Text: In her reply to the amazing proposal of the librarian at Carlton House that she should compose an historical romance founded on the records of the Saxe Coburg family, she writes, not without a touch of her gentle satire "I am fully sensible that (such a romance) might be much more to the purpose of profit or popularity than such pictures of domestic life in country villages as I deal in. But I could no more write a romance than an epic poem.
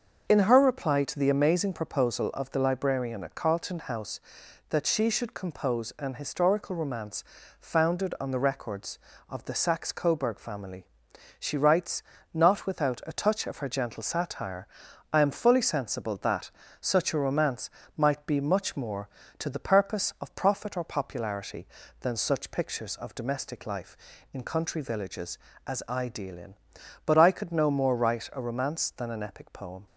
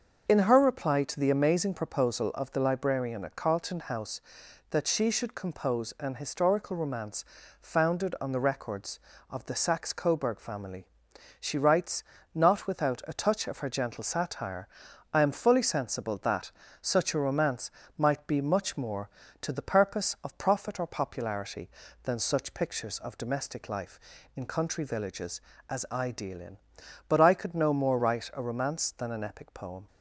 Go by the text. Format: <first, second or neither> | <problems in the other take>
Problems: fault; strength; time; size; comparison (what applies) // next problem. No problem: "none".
neither | starts louder than the rest; the same in both // pauses between "romance" and "founded"; slight; the same in both // pauses between "satire" and "I"; the same in both